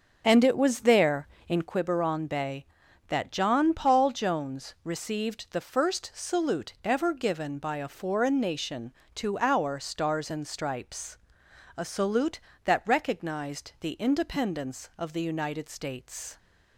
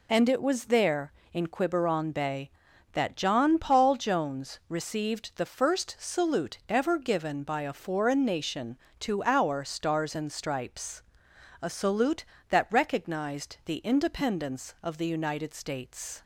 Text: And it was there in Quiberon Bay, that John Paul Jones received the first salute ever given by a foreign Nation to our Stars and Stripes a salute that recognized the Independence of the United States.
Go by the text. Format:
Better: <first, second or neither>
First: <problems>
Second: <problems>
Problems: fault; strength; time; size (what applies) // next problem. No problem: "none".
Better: second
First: starts louder than the rest; until 1.7 s; 6.5 dB // pauses between "Stripes" and "a"; noticeable; at 11.1 s; 0.60 s long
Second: pauses between "Stripes" and "a"; noticeable; at 11.0 s; 0.60 s long